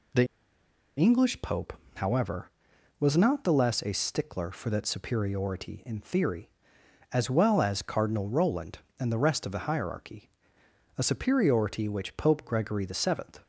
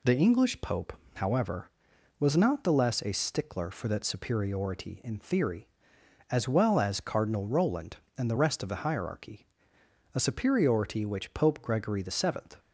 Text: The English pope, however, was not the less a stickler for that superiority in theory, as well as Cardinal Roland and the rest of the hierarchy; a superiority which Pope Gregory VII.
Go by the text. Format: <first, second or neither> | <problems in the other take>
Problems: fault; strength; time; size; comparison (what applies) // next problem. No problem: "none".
second | pauses between "The" and "English"; noticeable; at 0.2 s; 0.71 s long